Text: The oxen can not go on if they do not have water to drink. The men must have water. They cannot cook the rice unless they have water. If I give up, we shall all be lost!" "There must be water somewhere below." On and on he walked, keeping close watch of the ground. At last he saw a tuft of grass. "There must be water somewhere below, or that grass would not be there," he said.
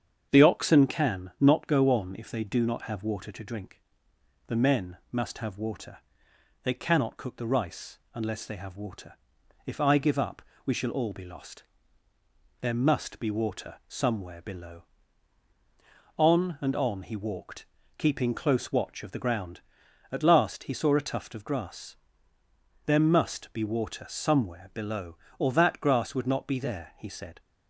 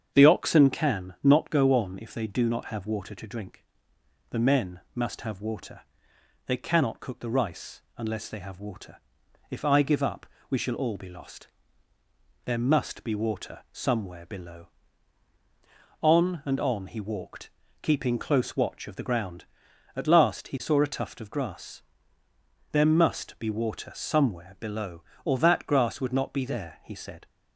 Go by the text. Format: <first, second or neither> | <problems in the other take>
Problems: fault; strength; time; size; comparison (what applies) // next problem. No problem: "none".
neither | starts louder than the rest; strong; the same in both // pauses between "rice" and "unless"; slight; the same in both